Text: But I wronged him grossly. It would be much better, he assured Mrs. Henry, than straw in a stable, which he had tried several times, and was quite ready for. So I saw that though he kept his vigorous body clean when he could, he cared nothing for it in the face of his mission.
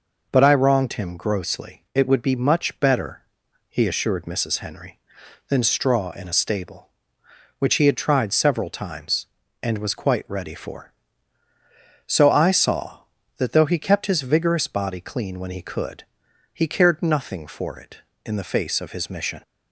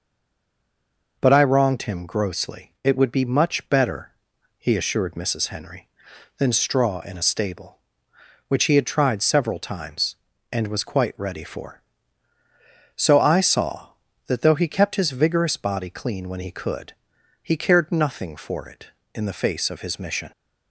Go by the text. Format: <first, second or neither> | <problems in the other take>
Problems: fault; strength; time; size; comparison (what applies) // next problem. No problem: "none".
first | stays silent before the first word; noticeable; until 1.1 s; 1.1 s long